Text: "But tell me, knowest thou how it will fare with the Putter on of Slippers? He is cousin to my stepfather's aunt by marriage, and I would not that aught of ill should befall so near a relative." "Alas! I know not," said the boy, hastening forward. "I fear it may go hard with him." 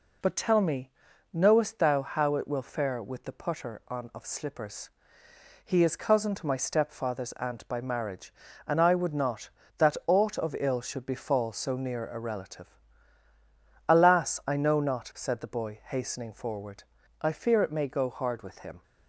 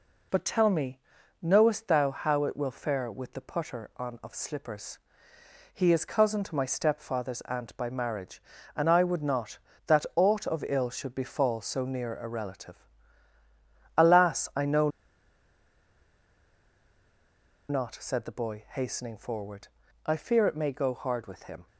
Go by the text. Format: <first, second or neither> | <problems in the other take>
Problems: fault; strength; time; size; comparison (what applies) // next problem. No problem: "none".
first | pauses between "know" and "not"; strong; at 14.8 s; 2.8 s long